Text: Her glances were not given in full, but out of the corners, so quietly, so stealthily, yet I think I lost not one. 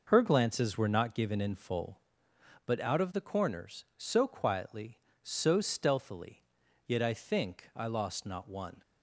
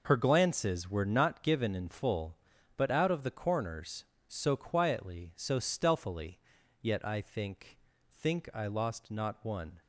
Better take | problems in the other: first | says "think" twice; at 8.1 s

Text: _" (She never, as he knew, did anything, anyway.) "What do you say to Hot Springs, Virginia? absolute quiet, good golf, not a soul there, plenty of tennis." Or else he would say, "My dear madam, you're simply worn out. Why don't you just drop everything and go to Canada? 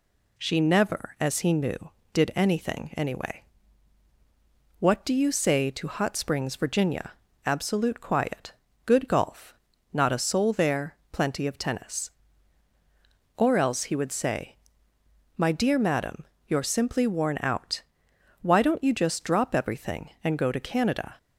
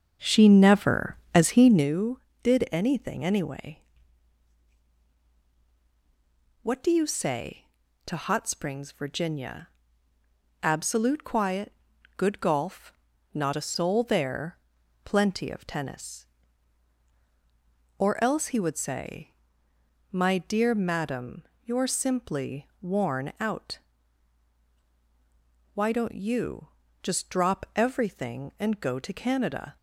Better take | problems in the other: first | starts louder than the rest; until 2.0 s; 7 dB // pauses between "you" and "just"; slight; at 26.6 s; 0.34 s long

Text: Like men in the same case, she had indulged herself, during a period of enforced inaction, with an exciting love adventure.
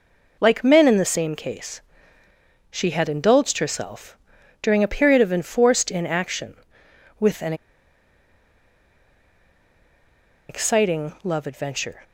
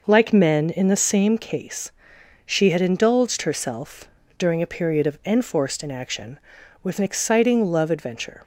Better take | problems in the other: second | pauses between "an" and "exciting"; strong; at 7.5 s; 2.9 s long

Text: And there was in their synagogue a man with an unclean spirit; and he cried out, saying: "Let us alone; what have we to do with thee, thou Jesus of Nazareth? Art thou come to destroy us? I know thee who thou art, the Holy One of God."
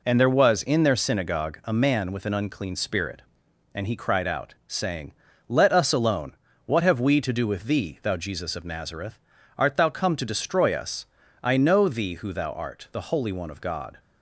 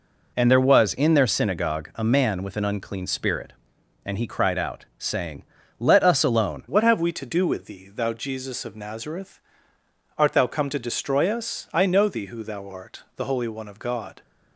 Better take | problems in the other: first | changes voice at "what"; from 6.6 s on; 7.6 s long

